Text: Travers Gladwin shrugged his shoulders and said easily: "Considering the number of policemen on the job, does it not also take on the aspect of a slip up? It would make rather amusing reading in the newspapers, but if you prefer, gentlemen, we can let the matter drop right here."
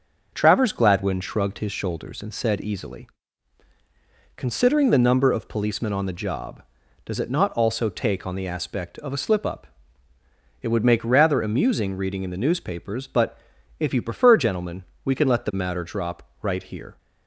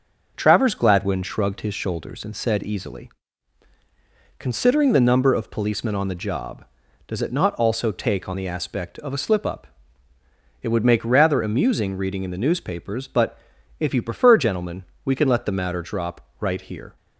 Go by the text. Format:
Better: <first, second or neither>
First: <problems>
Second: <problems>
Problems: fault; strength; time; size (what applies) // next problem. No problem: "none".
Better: neither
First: pauses between "but" and "if"; at 13.3 s; 0.40 s long // pauses between "drop" and "right"; slight; at 16.2 s; 0.20 s long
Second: pauses between "but" and "if"; at 13.3 s; 0.40 s long // pauses between "drop" and "right"; slight; at 16.1 s; 0.20 s long